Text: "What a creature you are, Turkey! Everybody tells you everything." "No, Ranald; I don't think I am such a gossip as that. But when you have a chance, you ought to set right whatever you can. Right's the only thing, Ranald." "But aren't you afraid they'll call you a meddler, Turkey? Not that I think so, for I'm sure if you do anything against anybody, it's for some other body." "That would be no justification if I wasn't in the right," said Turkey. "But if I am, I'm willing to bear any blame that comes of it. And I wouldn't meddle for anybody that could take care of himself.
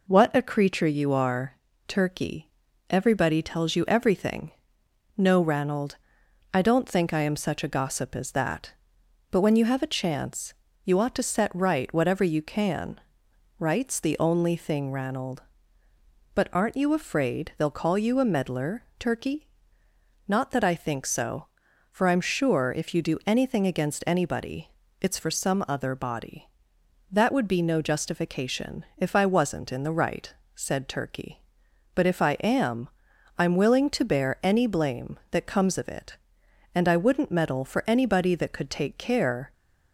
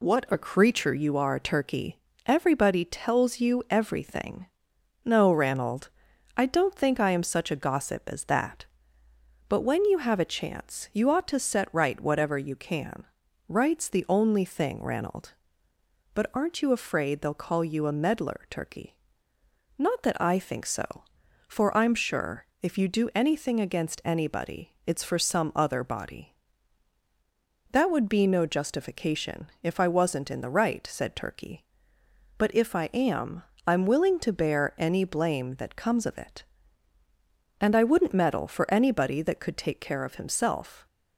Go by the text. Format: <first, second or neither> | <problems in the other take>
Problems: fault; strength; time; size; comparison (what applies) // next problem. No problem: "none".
second | stops before "of himself"; at 39.5 s